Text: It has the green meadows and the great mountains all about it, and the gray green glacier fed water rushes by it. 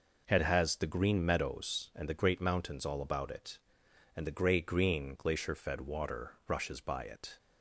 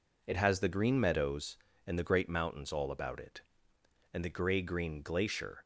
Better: first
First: none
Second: stops before "fed water rushes by it"; at 5.6 s

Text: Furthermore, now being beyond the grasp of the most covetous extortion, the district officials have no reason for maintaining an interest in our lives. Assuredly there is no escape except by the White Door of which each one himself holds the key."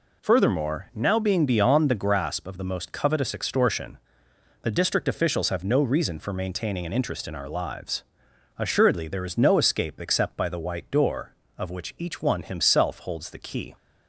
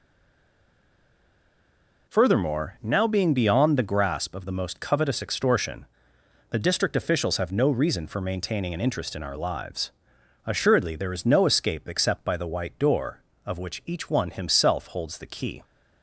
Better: first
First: none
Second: stays silent before the first word; until 2.0 s; 2.0 s long

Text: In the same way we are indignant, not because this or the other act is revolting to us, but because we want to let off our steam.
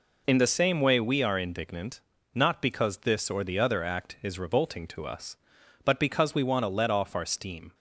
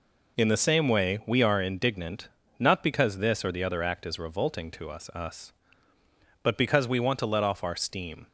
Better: first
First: none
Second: says "us" twice; at 5.1 s

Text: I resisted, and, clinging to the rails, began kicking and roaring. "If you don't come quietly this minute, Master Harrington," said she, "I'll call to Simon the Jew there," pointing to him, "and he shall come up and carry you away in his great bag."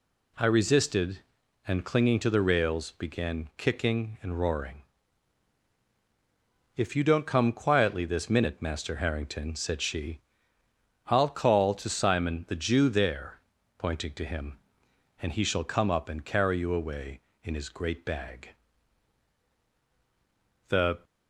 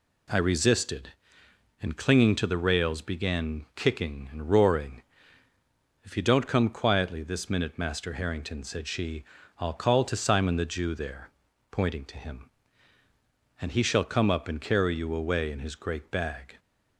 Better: second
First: goes on to say "The"; slight; from 20.6 s on; 0.34 s long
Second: none

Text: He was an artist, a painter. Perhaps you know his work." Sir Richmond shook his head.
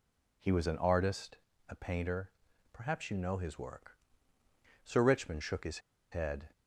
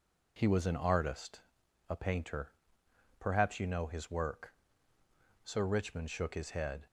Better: second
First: pauses between "his" and "head"; slight; at 5.7 s; 0.31 s long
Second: none

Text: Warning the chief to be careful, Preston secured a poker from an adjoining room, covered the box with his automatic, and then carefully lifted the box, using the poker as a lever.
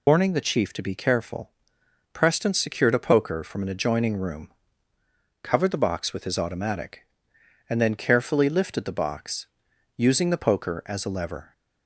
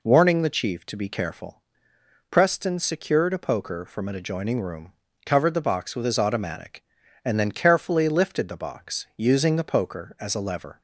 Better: second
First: loses the start of "Warning"; at 0.0 s; 70 ms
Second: none

